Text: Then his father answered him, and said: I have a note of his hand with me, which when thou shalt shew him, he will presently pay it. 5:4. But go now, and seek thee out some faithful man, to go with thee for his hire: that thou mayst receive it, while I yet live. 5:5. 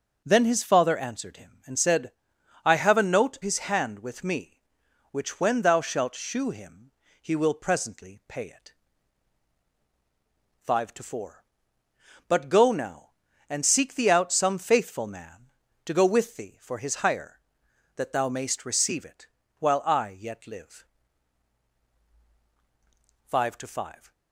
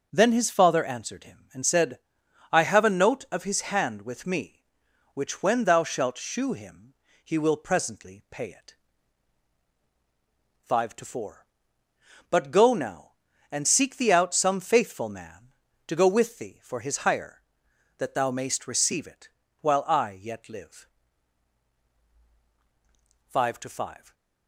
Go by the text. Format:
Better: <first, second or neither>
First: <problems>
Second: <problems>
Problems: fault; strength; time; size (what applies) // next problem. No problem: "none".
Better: second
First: starts louder than the rest; until 1.2 s; 6.5 dB // skips "of"; at 3.4 s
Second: none